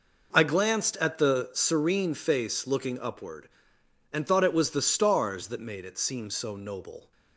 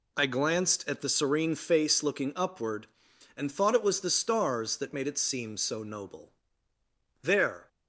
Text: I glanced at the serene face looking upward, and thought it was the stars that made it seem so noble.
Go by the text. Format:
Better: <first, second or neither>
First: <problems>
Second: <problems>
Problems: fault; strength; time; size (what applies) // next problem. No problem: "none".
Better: first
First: none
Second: goes on to say "There"; slight; from 7.2 s on; 0.46 s long